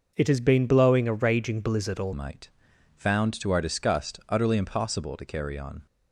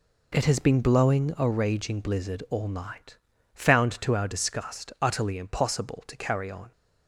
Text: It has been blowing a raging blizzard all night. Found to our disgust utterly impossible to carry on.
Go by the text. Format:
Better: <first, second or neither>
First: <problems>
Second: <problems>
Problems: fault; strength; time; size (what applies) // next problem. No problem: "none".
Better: second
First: changes voice at "night"; from 2.1 s on; 3.7 s long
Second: none